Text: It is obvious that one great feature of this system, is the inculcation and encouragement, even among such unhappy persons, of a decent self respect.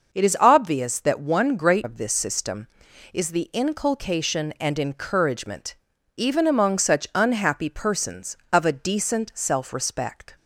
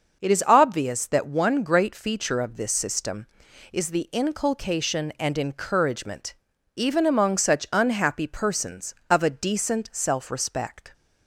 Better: second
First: skips "feature"; at 1.8 s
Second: none

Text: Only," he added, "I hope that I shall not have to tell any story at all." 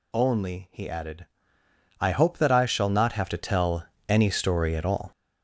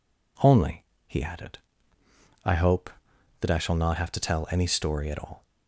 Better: second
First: gets louder; throughout; 7 dB // pauses between "tell" and "any"; slight; at 3.8 s; 0.24 s long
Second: none

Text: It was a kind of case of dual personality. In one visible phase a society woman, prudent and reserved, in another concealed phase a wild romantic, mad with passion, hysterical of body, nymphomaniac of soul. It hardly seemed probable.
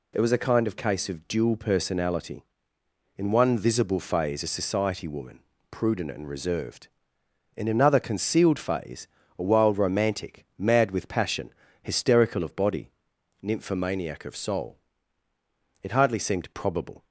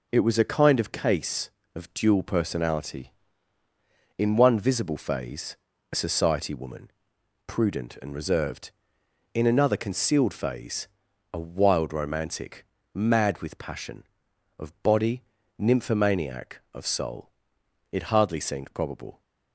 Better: first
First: pauses between "phase" and "a"; slight; at 9.0 s; 0.28 s long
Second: pauses between "phase" and "a"; slight; at 5.5 s; 0.36 s long // pauses between "phase" and "a"; noticeable; at 10.8 s; 0.46 s long // skips "hysterical"; at 14.3 s

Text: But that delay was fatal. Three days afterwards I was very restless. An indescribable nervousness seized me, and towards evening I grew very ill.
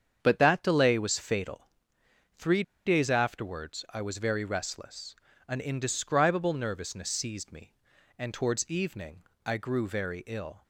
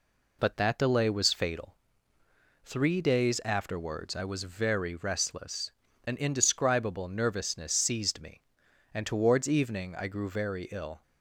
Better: second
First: starts louder than the rest; strong; until 1.2 s; 7.5 dB // pauses between "Three" and "days"; slight; at 2.6 s; 0.23 s long // pauses between "evening" and "I"; slight; at 9.2 s; 0.24 s long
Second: none

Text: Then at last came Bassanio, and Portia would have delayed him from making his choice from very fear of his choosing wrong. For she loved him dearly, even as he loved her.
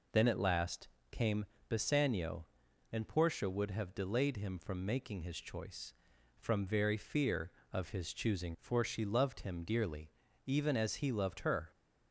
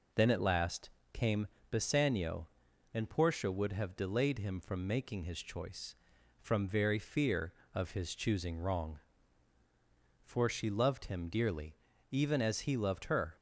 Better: second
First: pauses between "last" and "came"; slight; at 0.8 s; 0.22 s long // pauses between "came" and "Bassanio"; slight; at 1.4 s; 0.22 s long // skips "wrong"; at 8.5 s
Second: pauses between "last" and "came"; slight; at 0.8 s; 0.22 s long // pauses between "came" and "Bassanio"; slight; at 1.4 s; 0.22 s long

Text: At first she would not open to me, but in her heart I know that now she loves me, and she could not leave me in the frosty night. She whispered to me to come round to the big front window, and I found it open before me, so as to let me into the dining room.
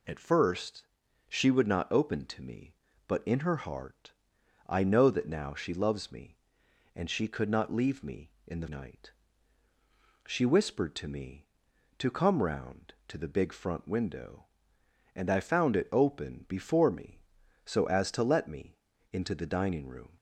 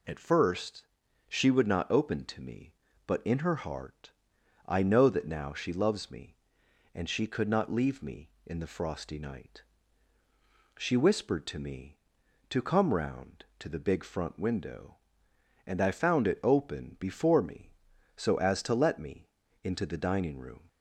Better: second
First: pauses between "first" and "she"; at 0.8 s; 0.44 s long // pauses between "heart" and "I"; noticeable; at 4.1 s; 0.54 s long // skips "frosty"; at 8.6 s // pauses between "me" and "into"; at 18.7 s; 0.38 s long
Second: pauses between "first" and "she"; at 0.8 s; 0.44 s long // pauses between "heart" and "I"; noticeable; at 4.1 s; 0.54 s long // pauses between "me" and "into"; at 19.2 s; 0.38 s long

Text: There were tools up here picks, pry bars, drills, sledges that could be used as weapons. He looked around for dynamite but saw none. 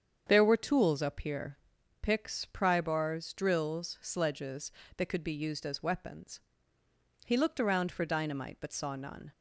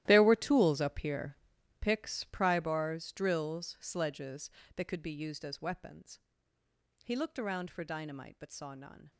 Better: first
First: starts louder than the rest; strong; until 1.2 s; 7.5 dB // pauses between "here" and "picks"; at 1.5 s; 0.44 s long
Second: gets quieter; strong; throughout; 15.5 dB // starts louder than the rest; strong; until 1.0 s; 13.5 dB // pauses between "here" and "picks"; at 1.3 s; 0.44 s long

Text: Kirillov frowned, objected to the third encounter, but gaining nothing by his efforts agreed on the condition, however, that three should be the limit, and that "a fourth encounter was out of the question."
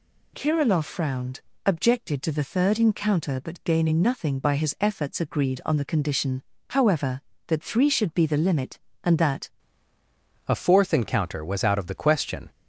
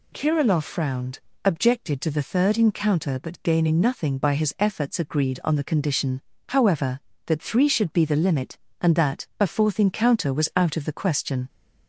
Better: second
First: changes voice at "a"; from 10.4 s on; 2.0 s long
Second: none

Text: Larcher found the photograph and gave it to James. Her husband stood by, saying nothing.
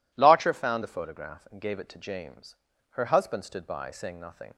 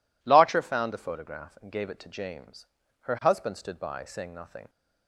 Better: neither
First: none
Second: none

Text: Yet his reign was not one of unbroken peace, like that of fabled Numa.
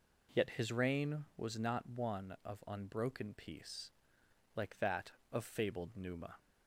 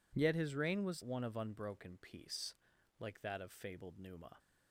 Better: first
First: none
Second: skips "not"; at 1.0 s

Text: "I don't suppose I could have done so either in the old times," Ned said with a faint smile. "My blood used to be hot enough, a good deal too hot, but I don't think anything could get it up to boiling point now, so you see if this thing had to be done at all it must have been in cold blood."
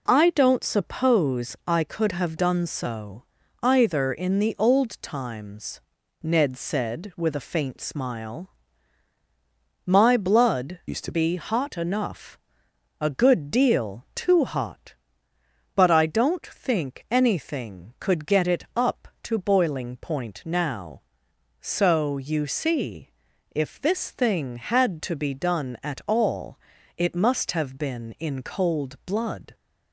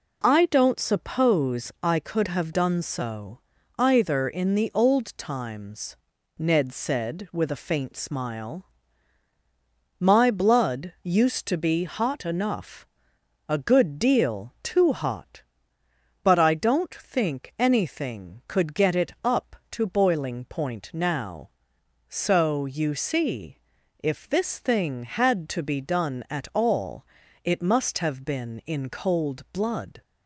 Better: second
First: pauses between "so" and "either"; slight; at 3.2 s; 0.36 s long // changes voice from "used" to "to"; from 10.8 to 11.1 s; 0.3 s long // pauses between "see" and "if"; at 23.0 s; 0.44 s long // pauses between "all" and "it"; at 26.5 s; 0.40 s long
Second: pauses between "so" and "either"; slight; at 3.4 s; 0.36 s long // pauses between "see" and "if"; at 23.5 s; 0.44 s long // pauses between "all" and "it"; at 27.0 s; 0.40 s long

